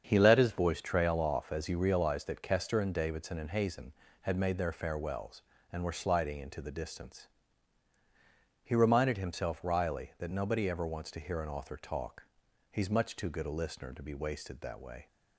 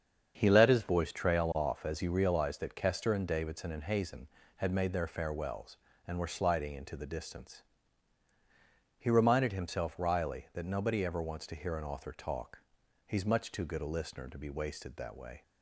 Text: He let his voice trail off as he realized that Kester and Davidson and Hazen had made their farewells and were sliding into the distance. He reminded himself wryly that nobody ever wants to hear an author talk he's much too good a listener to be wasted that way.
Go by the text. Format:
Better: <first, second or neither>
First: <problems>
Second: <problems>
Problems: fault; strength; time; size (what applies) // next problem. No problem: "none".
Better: neither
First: starts louder than the rest; strong; until 1.0 s; 7 dB // pauses between "talk" and "he's"; at 12.2 s; 0.44 s long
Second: starts louder than the rest; strong; until 1.3 s; 7 dB // pauses between "talk" and "he's"; at 12.6 s; 0.44 s long